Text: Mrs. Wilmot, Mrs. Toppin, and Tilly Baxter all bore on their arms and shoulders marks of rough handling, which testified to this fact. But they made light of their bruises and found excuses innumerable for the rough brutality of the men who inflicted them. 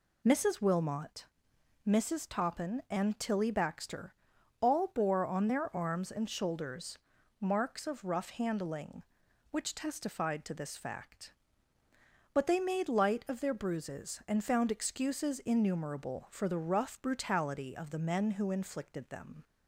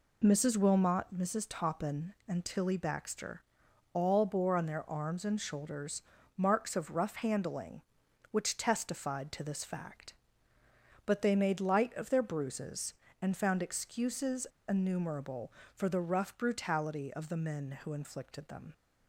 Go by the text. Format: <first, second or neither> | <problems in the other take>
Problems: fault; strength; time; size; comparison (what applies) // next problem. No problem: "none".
first | pauses between "Baxter" and "all"; noticeable; at 3.4 s; 0.50 s long; noticeable in the first // pauses between "shoulders" and "marks"; slight; at 6.0 s; 0.36 s long; also in the first // pauses between "excuses" and "innumerable"; slight; at 14.4 s; 0.21 s long